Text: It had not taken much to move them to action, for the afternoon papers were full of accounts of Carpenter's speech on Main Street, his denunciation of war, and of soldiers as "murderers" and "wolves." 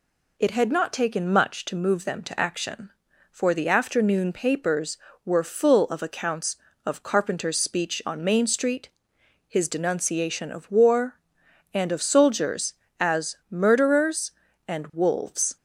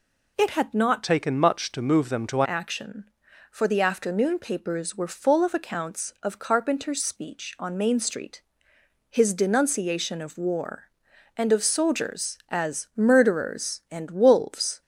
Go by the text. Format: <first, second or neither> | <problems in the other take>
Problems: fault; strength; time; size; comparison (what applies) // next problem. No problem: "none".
first | changes voice from "taken" to "to"; from 1.0 to 2.4 s; 1.4 s long